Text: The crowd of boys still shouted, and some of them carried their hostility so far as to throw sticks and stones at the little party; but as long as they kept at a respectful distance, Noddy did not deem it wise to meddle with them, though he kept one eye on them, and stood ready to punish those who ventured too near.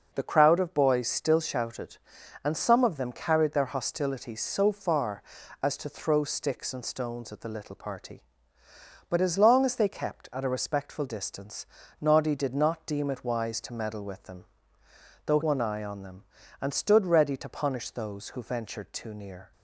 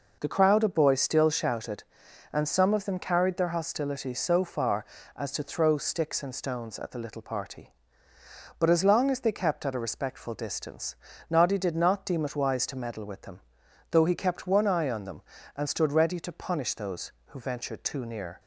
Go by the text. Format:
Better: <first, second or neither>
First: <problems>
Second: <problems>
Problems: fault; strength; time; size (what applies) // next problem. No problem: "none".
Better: second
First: skips "he kept"; at 15.4 s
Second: none